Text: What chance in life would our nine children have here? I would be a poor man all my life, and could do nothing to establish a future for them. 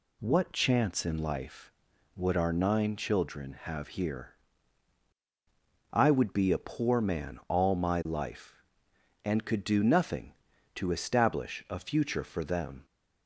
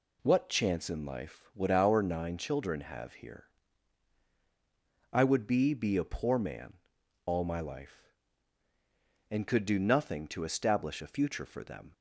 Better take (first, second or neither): first